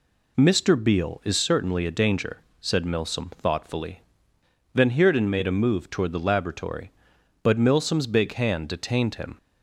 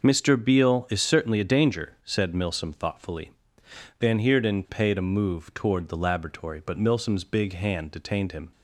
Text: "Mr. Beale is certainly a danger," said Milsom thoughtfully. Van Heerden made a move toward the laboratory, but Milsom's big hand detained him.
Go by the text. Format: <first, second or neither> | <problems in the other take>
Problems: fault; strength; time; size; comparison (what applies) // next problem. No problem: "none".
first | says "paid" for "made"; at 4.6 s